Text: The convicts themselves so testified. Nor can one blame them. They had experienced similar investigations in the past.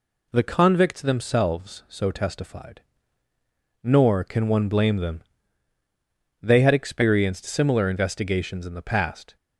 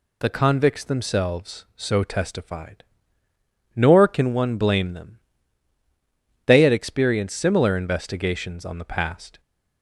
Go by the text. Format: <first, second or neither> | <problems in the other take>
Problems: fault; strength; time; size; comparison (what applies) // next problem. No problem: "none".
first | says "on" for "in"; at 8.6 s